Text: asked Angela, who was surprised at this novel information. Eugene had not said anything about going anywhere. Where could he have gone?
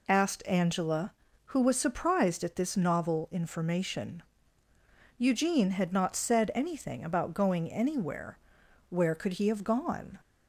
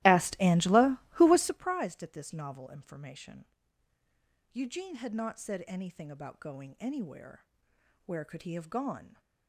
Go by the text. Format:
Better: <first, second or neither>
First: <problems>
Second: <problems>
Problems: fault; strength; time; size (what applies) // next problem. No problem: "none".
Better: first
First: none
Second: starts louder than the rest; strong; until 1.7 s; 16.5 dB